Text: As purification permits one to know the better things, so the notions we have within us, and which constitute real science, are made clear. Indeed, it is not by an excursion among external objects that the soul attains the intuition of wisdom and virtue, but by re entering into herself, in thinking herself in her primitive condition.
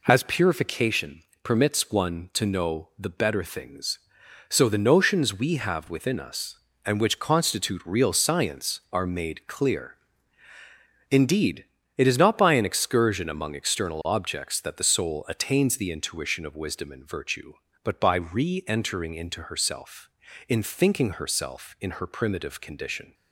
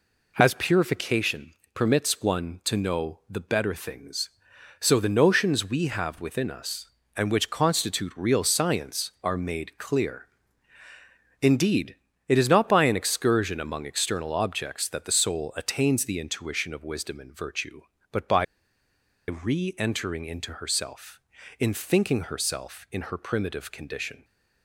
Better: first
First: pauses between "purification" and "permits"; slight; at 1.2 s; 0.22 s long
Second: pauses between "purification" and "permits"; slight; at 1.5 s; 0.22 s long // pauses between "by" and "re"; noticeable; at 18.4 s; 0.84 s long

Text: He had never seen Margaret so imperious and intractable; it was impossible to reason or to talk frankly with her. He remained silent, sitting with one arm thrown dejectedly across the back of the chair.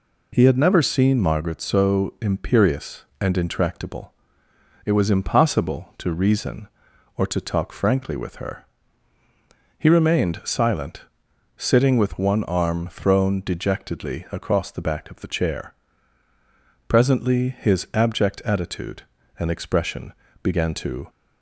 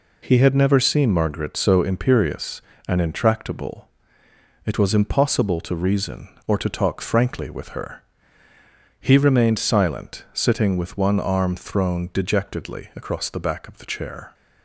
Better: second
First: goes on to say "Presently his abject attitude and expression began to"; strong; from 16.8 s on; 4.2 s long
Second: none

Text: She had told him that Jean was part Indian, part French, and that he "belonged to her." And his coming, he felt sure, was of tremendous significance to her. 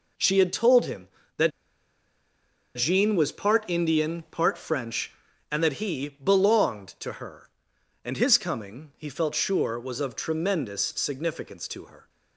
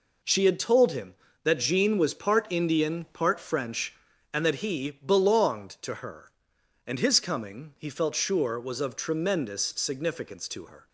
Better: second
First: pauses between "that" and "Jean"; strong; at 1.5 s; 1.2 s long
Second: none

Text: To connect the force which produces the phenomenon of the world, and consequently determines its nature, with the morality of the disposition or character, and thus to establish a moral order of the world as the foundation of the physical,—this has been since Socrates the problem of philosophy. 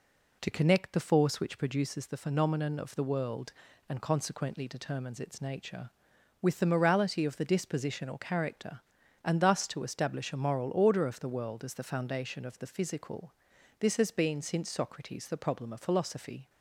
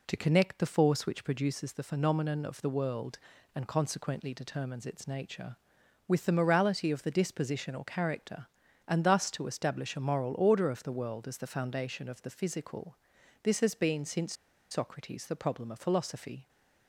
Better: first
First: none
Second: pauses between "since" and "Socrates"; at 14.3 s; 0.37 s long

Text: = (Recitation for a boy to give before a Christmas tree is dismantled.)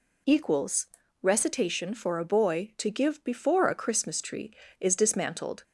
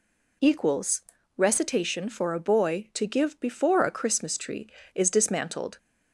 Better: neither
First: none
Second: none

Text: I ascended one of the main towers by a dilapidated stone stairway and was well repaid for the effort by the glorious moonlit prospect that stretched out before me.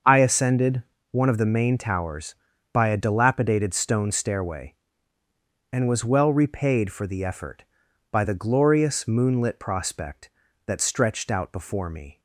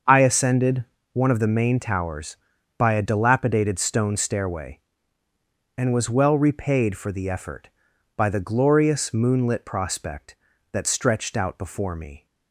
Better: neither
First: starts louder than the rest; until 1.3 s; 6.5 dB // pauses between "ascended" and "one"; slight; at 0.8 s; 0.28 s long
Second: starts louder than the rest; until 1.3 s; 6.5 dB // pauses between "ascended" and "one"; slight; at 0.8 s; 0.28 s long

